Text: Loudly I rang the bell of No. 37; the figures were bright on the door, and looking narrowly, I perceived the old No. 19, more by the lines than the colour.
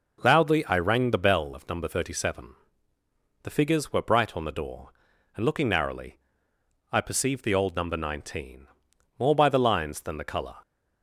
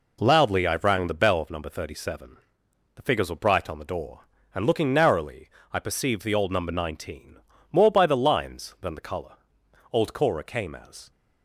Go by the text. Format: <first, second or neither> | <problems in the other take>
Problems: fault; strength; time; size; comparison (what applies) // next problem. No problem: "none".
first | goes on to say "Old Cora came as"; noticeable; from 9.9 s on; 1.1 s long